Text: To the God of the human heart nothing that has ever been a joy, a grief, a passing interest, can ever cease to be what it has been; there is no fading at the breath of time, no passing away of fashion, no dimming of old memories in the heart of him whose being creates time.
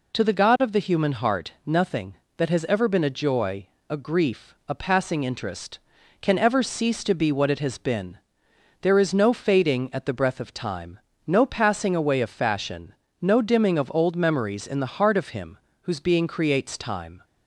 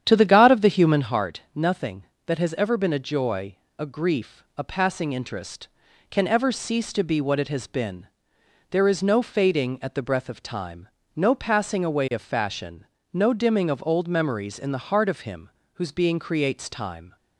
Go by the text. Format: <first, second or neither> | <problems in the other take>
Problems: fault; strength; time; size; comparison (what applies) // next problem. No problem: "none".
first | starts louder than the rest; strong; until 1.2 s; 9.5 dB // pauses between "him" and "whose"; slight; at 15.4 s; 0.24 s long; slight in the first